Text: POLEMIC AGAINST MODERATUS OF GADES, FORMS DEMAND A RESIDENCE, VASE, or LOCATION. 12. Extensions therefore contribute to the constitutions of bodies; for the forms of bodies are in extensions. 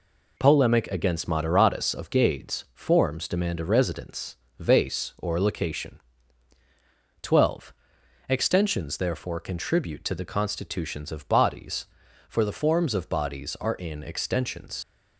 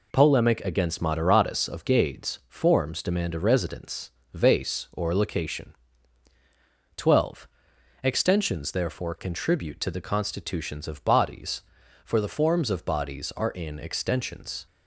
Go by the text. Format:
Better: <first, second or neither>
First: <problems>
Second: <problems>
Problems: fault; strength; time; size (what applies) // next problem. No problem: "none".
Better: second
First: leaves "extensions" unfinished; at 14.8 s; 70 ms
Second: none